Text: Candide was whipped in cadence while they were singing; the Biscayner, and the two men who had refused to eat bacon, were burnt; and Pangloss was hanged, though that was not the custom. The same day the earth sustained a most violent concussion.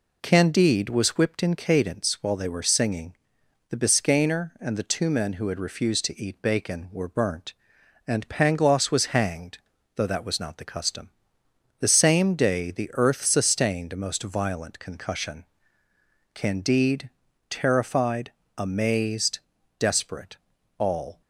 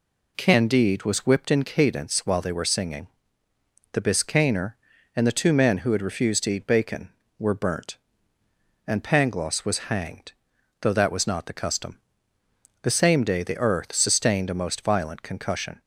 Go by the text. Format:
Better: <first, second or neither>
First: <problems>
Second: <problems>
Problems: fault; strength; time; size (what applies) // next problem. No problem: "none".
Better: second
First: goes on to say "Candide terrified amazed desperate all"; strong; from 16.3 s on; 4.8 s long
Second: none